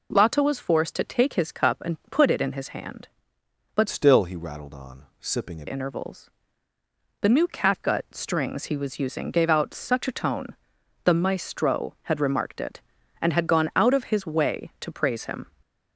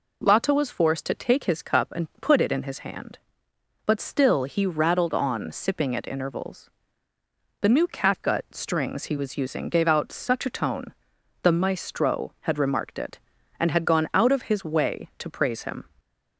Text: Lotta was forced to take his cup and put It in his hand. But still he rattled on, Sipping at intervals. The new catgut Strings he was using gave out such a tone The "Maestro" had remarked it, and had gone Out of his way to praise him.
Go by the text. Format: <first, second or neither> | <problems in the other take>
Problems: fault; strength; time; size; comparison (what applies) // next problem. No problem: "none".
second | changes voice from "still" to "at"; from 3.8 to 5.6 s; 1.8 s long // pauses between "tone" and "The"; noticeable; at 10.5 s; 0.50 s long; noticeable in the second